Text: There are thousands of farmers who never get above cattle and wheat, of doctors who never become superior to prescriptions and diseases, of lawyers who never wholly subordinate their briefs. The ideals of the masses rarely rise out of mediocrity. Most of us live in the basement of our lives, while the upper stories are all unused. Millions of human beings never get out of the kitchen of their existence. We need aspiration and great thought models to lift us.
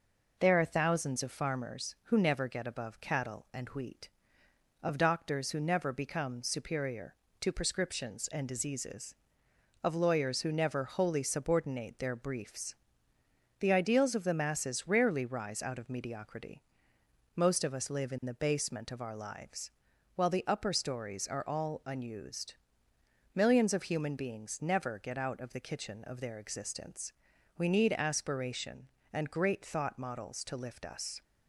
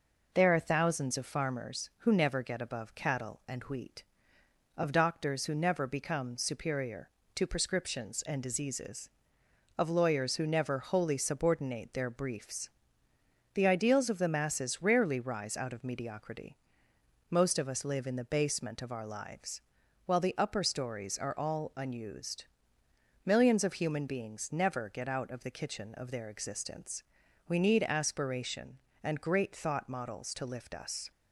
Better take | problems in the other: neither | none

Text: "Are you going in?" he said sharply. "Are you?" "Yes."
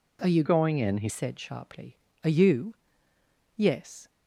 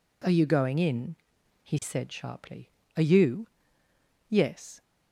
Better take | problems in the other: second | changes voice from "going" to "he"; from 0.4 to 1.0 s; 0.6 s long

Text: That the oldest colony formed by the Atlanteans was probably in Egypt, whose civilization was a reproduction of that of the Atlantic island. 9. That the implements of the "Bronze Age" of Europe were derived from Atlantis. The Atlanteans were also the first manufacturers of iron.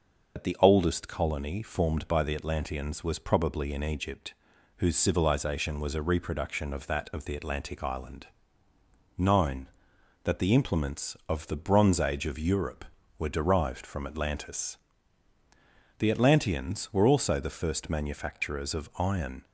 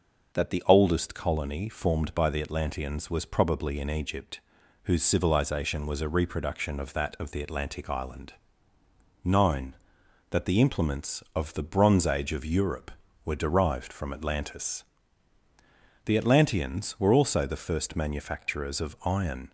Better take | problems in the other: second | loses the start of "That"; at 0.3 s; 80 ms

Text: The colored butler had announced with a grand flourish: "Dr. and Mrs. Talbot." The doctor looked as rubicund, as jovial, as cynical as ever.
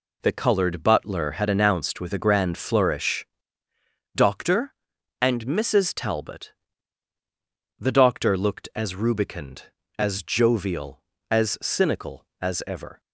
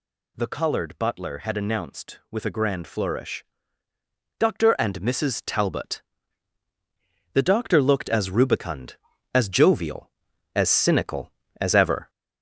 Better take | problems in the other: first | gets louder; throughout; 4 dB

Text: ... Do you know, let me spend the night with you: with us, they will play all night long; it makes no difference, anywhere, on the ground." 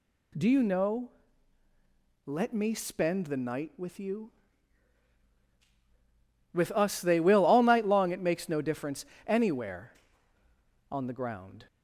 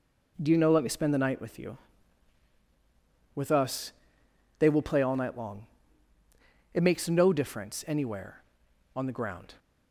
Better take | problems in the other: second | skips "play"; at 7.4 s

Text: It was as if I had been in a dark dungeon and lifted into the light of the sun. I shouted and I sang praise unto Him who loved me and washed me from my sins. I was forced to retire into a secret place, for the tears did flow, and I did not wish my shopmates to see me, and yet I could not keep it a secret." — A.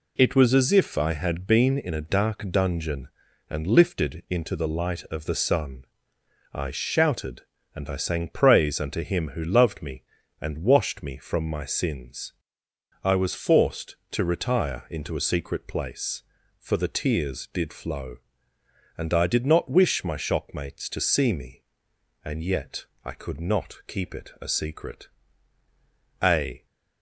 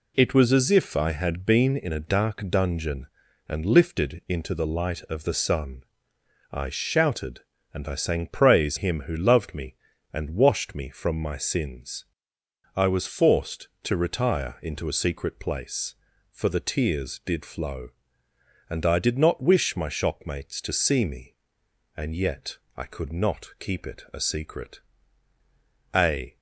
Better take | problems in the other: first | skips "unto"; at 8.7 s // pauses between "yet" and "I"; slight; at 22.5 s; 0.18 s long; slight in the first

